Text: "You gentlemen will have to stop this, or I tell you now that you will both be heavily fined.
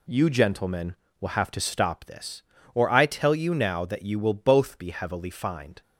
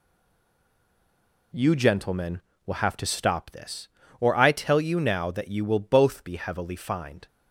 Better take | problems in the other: first | stays silent before the first word; noticeable; until 1.5 s; 1.5 s long

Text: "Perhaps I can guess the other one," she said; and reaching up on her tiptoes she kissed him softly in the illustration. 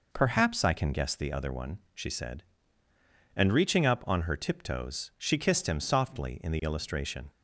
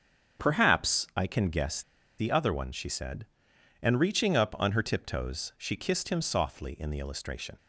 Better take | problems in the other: first | starts louder than the rest; strong; until 1.4 s; 7.5 dB // pauses between "guess" and "the"; slight; at 1.8 s; 0.35 s long

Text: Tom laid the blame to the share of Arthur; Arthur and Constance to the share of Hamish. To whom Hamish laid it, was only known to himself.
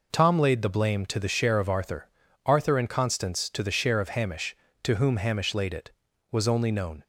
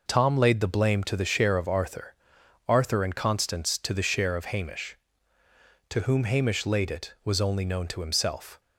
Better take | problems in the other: second | stops before "to himself"; at 7.0 s

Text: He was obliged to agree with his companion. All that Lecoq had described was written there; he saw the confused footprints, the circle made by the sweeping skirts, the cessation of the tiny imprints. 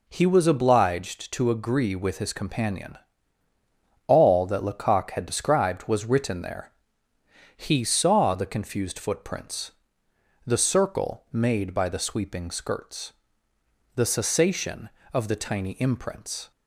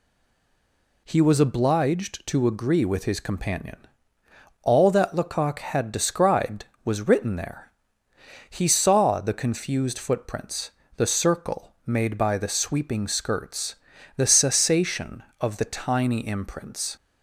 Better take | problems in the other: first | stays silent before the first word; until 1.0 s; 1.0 s long

